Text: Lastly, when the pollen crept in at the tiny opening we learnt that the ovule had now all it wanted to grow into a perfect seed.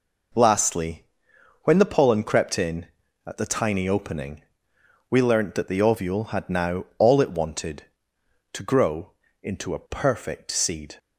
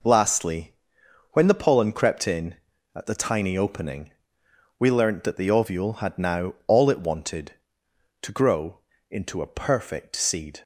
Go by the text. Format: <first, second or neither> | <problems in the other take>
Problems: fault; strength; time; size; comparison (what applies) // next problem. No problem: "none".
neither | pauses between "opening" and "we"; noticeable; the same in both // pauses between "grow" and "into"; slight; the same in both